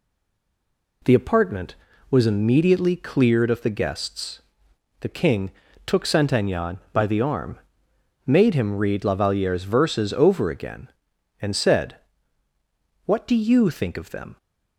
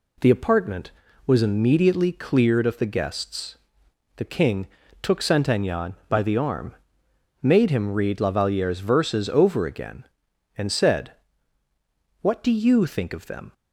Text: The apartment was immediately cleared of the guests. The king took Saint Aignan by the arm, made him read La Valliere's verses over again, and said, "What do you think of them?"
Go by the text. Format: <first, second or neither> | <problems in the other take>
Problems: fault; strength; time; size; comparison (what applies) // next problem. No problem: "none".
second | stays silent before the first word; until 1.0 s; 1.0 s long // pauses between "king" and "took"; slight; at 5.5 s; 0.34 s long; slight in the second